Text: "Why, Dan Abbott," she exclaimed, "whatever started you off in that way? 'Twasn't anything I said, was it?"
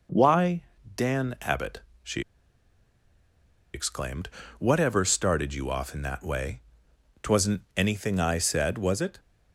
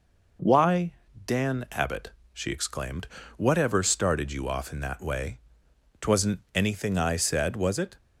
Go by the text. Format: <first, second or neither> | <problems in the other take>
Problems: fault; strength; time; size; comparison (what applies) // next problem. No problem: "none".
second | pauses between "she" and "exclaimed"; strong; at 2.2 s; 1.5 s long // pauses between "Twasn't" and "anything"; slight; at 7.6 s; 0.16 s long; slight in the second